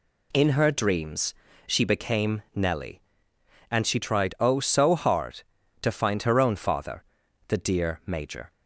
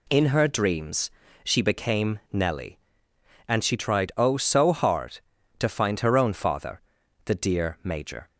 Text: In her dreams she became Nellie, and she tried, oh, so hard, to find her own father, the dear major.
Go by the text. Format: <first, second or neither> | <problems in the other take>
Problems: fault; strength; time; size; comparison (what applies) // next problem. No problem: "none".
neither | pauses between "dreams" and "she"; slight; the same in both